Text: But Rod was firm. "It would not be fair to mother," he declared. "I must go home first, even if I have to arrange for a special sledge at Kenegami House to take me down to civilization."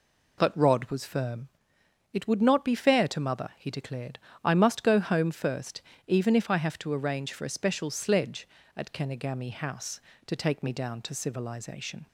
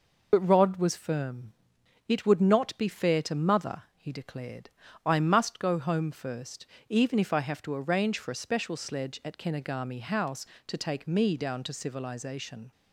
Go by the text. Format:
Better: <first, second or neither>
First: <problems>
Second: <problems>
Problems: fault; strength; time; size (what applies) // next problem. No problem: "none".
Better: first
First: none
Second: loses the start of "But"; at 0.3 s; 60 ms